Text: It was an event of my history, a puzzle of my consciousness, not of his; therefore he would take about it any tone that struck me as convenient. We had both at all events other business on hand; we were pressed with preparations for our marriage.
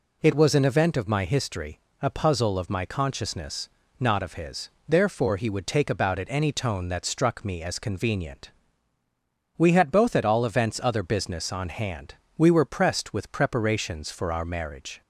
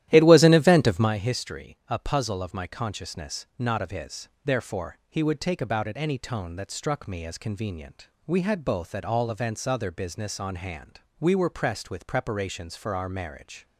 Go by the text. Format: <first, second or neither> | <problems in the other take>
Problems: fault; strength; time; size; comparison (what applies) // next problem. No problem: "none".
first | starts louder than the rest; strong; until 1.2 s; 13 dB